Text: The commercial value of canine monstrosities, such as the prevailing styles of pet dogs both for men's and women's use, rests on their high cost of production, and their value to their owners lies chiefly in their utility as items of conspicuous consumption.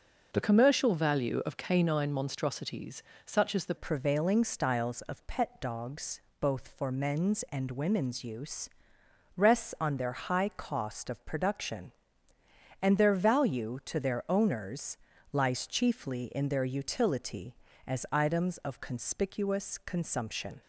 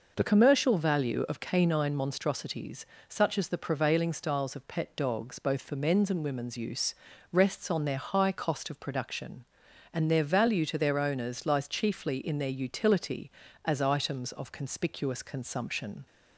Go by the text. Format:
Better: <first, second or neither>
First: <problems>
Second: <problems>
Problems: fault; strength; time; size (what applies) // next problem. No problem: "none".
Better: second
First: changes voice at "prevailing"; from 3.7 s on; 16.9 s long // pauses between "dogs" and "both"; slight; at 6.2 s; 0.18 s long // pauses between "owners" and "lies"; slight; at 14.9 s; 0.36 s long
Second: none